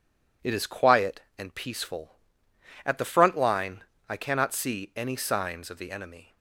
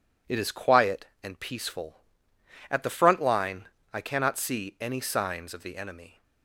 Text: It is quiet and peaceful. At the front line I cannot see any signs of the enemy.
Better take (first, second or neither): neither